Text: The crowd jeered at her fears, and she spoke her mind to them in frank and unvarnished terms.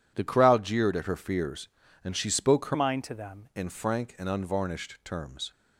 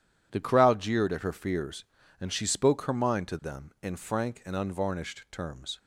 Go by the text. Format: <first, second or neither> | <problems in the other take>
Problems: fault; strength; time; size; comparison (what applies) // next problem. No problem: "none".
second | changes voice from "mind" to "them"; from 2.7 to 3.4 s; 0.7 s long